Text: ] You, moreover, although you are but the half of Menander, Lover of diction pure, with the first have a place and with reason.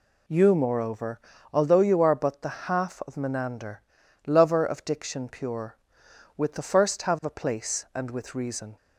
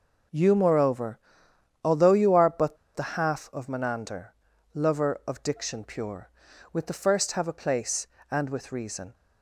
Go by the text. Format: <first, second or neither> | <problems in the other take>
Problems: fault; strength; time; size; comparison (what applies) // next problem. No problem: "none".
first | pauses between "but" and "the"; slight; at 2.7 s; 0.19 s long